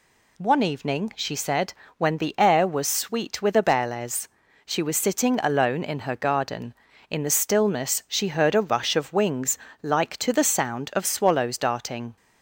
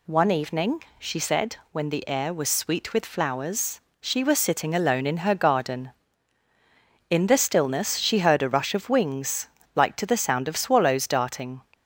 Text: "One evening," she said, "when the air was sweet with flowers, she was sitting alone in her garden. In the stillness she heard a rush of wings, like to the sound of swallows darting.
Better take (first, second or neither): second